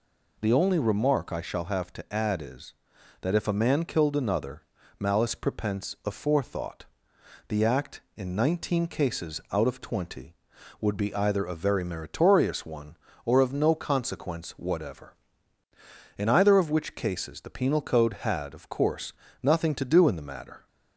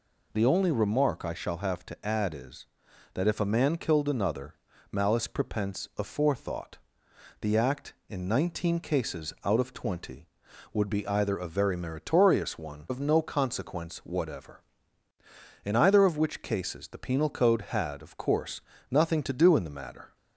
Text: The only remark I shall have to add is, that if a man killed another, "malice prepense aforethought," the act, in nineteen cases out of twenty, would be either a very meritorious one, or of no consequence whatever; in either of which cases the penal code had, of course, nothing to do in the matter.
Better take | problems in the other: first | skips "or"; at 12.8 s

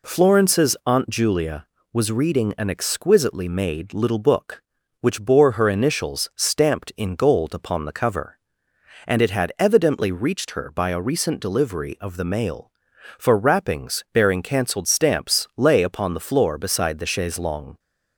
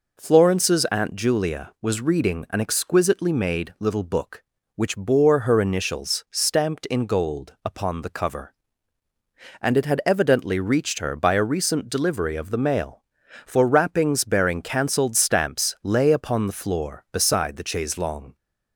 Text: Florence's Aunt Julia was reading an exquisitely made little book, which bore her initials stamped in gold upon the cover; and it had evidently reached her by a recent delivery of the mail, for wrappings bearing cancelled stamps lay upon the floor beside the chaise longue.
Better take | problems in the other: neither | none

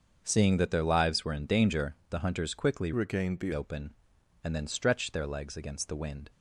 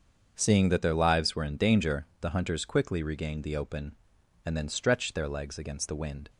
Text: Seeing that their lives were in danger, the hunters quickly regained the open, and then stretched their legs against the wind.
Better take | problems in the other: second | starts louder than the rest; until 1.2 s; 7 dB; also in the second // changes voice from "regained" to "the"; from 2.9 to 3.5 s; 0.6 s long

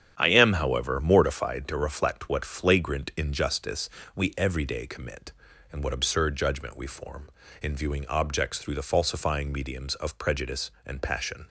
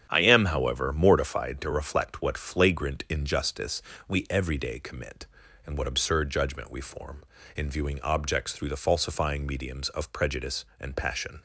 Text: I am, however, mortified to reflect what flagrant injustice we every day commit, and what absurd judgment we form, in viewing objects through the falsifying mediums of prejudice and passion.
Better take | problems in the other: neither | starts louder than the rest; strong; the same in both // pauses between "injustice" and "we"; slight; the same in both

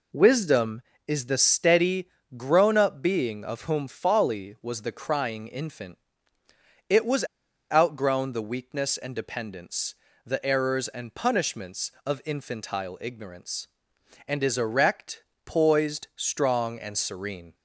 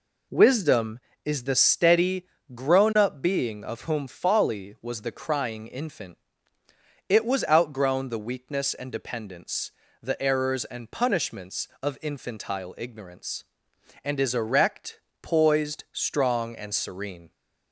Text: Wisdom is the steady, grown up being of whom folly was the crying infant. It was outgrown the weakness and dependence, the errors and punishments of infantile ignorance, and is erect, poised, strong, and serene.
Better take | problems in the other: second | pauses between "was" and "outgrown"; noticeable; at 7.2 s; 0.49 s long

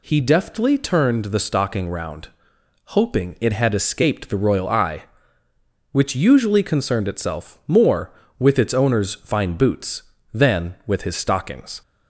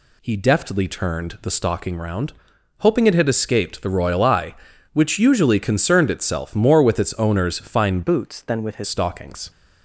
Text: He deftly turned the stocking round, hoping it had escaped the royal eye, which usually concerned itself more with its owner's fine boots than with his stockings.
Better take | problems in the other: first | changes voice from "boots" to "his"; from 8.0 to 8.8 s; 0.8 s long

